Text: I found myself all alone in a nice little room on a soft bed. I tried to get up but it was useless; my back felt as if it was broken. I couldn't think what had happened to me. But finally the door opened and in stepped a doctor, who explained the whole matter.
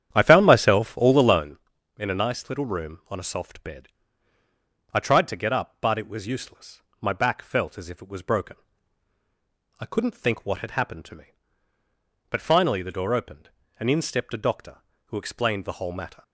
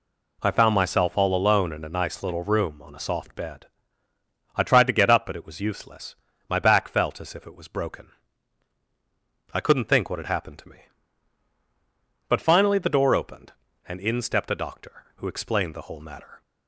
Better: second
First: starts louder than the rest; strong; until 1.6 s; 9.5 dB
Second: none

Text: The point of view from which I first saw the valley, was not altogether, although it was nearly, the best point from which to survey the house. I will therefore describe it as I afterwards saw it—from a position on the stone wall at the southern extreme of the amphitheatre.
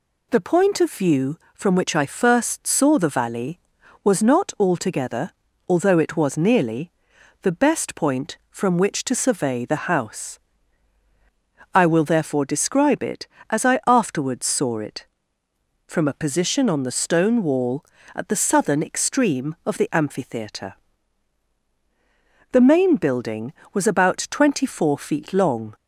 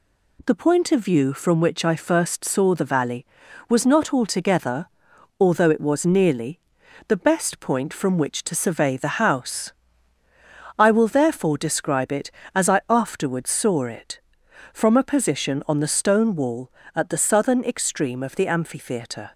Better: second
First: goes on to say "The main building was about twenty four feet long"; strong; from 22.5 s on; 3.2 s long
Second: none

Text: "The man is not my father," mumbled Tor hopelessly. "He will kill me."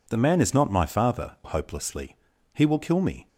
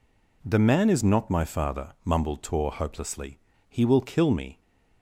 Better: second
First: skips "mumbled Tor"; at 1.4 s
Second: none

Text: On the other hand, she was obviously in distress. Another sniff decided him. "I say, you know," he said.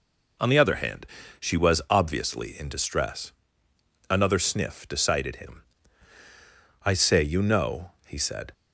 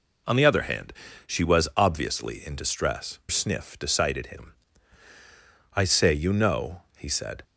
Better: first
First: none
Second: skips "Another"; at 3.2 s

